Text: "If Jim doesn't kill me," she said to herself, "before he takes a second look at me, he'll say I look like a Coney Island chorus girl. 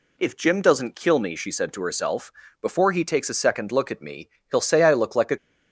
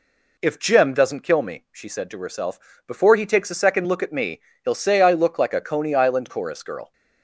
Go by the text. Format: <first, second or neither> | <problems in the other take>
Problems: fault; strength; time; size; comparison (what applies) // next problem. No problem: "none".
second | stops before "Coney Island chorus girl"; at 5.3 s